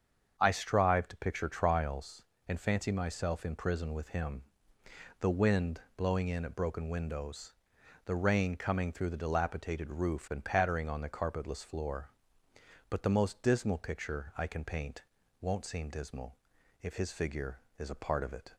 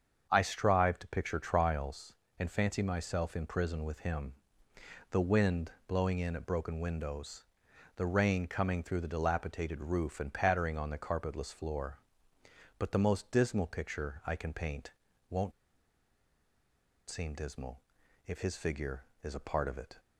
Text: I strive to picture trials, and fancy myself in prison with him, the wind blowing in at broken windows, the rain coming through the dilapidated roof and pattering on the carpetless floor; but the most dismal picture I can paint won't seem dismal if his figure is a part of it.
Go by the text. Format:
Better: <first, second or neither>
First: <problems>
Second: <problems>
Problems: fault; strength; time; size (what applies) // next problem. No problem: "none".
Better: first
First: starts louder than the rest; until 1.3 s; 7 dB // pauses between "wind" and "blowing"; slight; at 5.8 s; 0.16 s long // pauses between "paint" and "won't"; at 15.0 s; 0.38 s long // pauses between "dismal" and "if"; at 16.3 s; 0.44 s long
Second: starts louder than the rest; until 1.3 s; 7 dB // pauses between "wind" and "blowing"; slight; at 5.7 s; 0.16 s long // pauses between "paint" and "won't"; at 14.9 s; 0.38 s long // pauses between "won't" and "seem"; strong; at 15.5 s; 1.5 s long // pauses between "dismal" and "if"; at 17.8 s; 0.44 s long